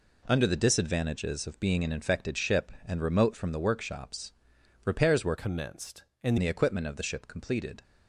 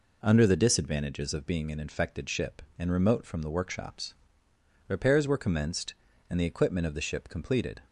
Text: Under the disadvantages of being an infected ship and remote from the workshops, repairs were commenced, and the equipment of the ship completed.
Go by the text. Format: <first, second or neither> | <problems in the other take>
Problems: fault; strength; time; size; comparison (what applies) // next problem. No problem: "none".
second | changes voice from "commenced" to "and"; from 5.3 to 6.3 s; 1.0 s long